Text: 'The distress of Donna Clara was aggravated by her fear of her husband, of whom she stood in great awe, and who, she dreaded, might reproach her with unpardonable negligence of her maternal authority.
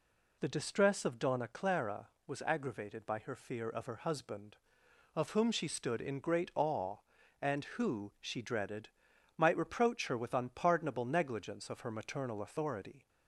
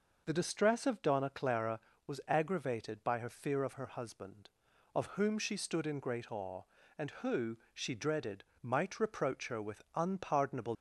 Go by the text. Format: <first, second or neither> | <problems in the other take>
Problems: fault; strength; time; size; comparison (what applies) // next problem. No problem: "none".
first | stops before "negligence of her maternal authority"; at 10.7 s